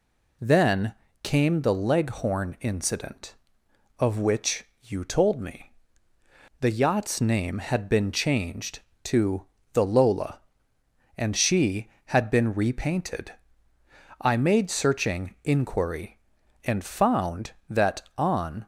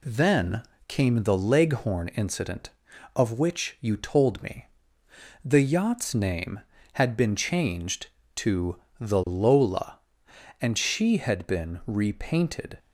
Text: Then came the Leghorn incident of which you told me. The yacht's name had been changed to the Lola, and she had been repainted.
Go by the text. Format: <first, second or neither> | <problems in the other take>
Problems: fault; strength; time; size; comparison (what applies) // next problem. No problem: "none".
second | pauses between "Then" and "came"; slight; at 0.9 s; 0.28 s long; slight in the second // pauses between "which" and "you"; slight; at 4.6 s; 0.16 s long // pauses between "to" and "the"; slight; at 9.4 s; 0.30 s long; slight in the second // goes on to say "I made searching inquiry and found that on"; strong; from 14.1 s on; 4.4 s long